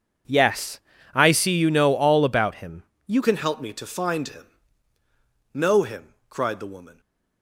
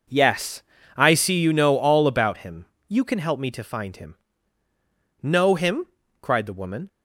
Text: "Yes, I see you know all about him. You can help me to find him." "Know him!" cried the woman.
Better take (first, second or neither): second